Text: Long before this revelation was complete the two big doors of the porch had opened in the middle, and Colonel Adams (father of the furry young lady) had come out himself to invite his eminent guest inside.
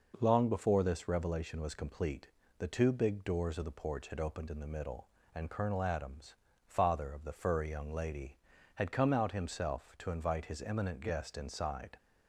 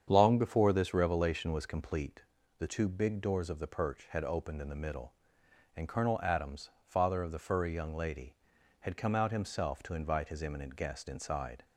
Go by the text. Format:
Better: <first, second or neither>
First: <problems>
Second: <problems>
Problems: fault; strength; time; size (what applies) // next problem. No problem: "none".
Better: first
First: pauses between "complete" and "the"; slight; at 2.2 s; 0.30 s long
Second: starts louder than the rest; strong; until 1.1 s; 8 dB // pauses between "complete" and "the"; slight; at 2.2 s; 0.36 s long // says "perch" for "porch"; at 3.6 s